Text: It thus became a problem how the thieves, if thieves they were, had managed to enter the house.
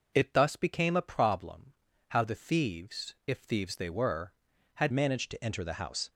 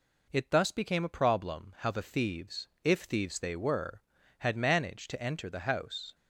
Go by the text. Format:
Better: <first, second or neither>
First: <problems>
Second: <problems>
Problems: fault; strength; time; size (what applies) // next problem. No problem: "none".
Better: second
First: pauses between "problem" and "how"; slight; at 1.7 s; 0.36 s long // changes voice at "managed"; from 4.8 s on; 1.2 s long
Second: none